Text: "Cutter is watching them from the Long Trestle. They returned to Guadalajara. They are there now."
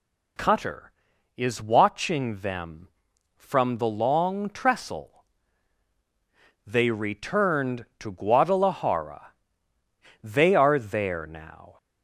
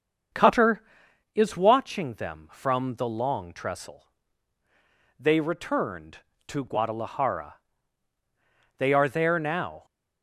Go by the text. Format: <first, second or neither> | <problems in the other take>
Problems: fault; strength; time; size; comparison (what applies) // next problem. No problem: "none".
first | starts louder than the rest; until 1.2 s; 7 dB